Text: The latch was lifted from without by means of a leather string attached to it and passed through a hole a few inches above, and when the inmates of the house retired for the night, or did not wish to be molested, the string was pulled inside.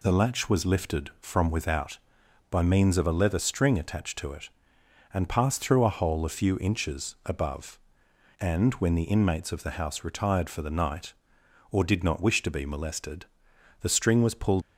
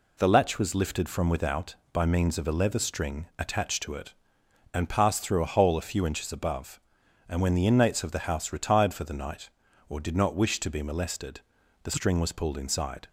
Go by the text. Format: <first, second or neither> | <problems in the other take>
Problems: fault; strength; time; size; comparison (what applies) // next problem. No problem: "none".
second | stops before "inside"; at 14.6 s